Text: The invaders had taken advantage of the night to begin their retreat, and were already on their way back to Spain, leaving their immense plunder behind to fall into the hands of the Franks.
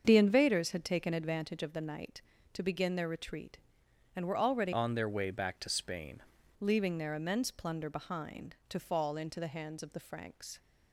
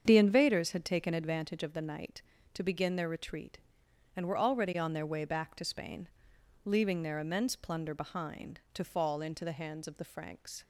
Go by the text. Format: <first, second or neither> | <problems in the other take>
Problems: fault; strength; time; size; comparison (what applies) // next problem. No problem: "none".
second | starts louder than the rest; until 1.0 s; 7 dB; strong in the second // changes voice from "on" to "Spain"; from 4.7 to 6.2 s; 1.5 s long